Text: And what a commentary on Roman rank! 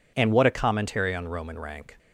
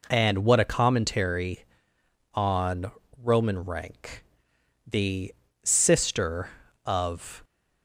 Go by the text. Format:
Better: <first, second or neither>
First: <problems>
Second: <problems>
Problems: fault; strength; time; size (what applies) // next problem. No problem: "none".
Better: first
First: none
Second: pauses between "on" and "Roman"; slight; at 2.8 s; 0.32 s long // goes on to say "The sister of"; strong; from 4.8 s on; 2.5 s long